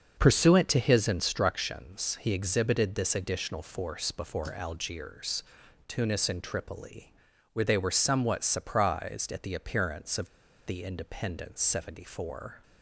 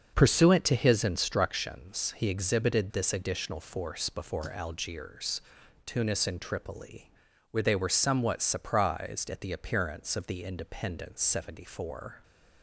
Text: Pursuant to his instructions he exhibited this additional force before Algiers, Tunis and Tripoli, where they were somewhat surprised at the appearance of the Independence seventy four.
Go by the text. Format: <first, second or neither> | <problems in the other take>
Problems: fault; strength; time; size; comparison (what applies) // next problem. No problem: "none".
second | starts louder than the rest; until 1.1 s; 6.5 dB; also in the second // pauses between "of" and "the"; at 10.2 s; 0.40 s long